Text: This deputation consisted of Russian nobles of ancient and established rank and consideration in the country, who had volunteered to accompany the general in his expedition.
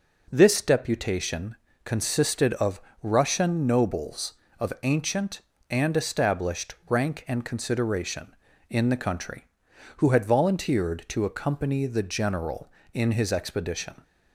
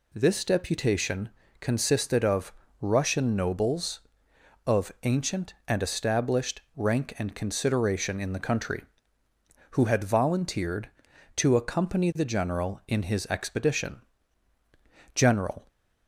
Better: first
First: pauses between "deputation" and "consisted"; slight; at 1.5 s; 0.30 s long // pauses between "of" and "Russian"; slight; at 2.8 s; 0.20 s long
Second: pauses between "deputation" and "consisted"; slight; at 1.3 s; 0.28 s long // pauses between "of" and "Russian"; slight; at 2.5 s; 0.28 s long // pauses between "established" and "rank"; slight; at 6.6 s; 0.16 s long // goes on to say "General"; from 15.1 s on; 0.54 s long

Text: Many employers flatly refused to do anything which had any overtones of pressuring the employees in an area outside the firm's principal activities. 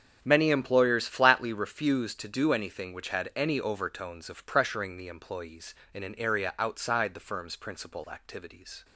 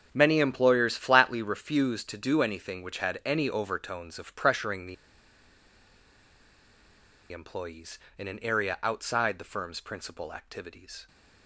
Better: first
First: starts louder than the rest; strong; until 1.2 s; 7 dB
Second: starts louder than the rest; until 1.1 s; 7 dB // pauses between "the" and "employees"; strong; at 4.9 s; 2.3 s long

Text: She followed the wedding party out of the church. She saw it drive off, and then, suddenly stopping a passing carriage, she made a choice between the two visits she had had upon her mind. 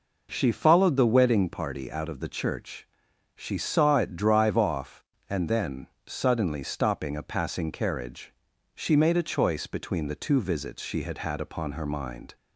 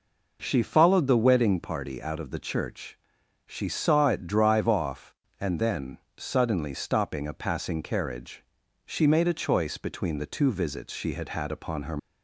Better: first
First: none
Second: stops before "mind"; at 11.9 s

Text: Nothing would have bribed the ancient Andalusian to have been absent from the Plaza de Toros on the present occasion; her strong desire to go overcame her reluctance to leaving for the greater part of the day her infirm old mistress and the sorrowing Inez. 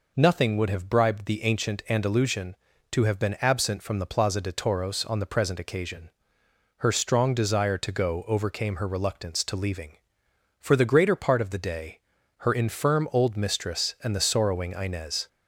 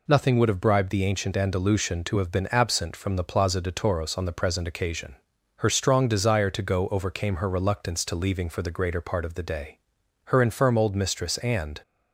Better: first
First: pauses between "day" and "her"; at 11.9 s; 0.44 s long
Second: pauses between "day" and "her"; noticeable; at 9.7 s; 0.46 s long // stops before "the sorrowing Inez"; at 11.8 s

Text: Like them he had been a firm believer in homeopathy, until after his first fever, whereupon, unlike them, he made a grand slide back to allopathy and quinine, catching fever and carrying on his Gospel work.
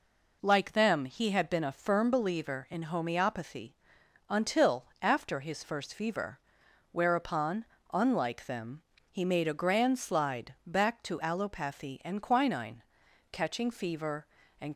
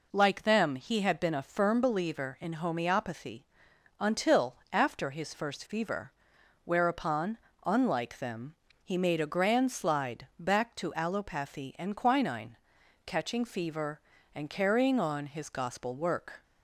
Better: second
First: pauses between "until" and "after"; slight; at 4.8 s; 0.16 s long // stops before "carrying on his Gospel work"; at 14.7 s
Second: pauses between "until" and "after"; slight; at 4.5 s; 0.16 s long

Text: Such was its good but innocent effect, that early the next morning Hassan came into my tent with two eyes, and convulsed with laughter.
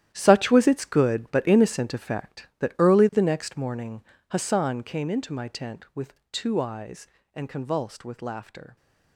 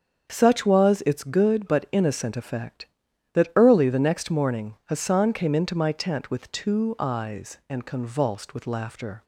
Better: second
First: gets quieter; strong; throughout; 12.5 dB // starts louder than the rest; strong; until 1.1 s; 11.5 dB // pauses between "morning" and "Hassan"; slight; at 4.0 s; 0.26 s long // pauses between "with" and "two"; slight; at 6.1 s; 0.16 s long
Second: starts louder than the rest; strong; until 1.3 s; 7 dB

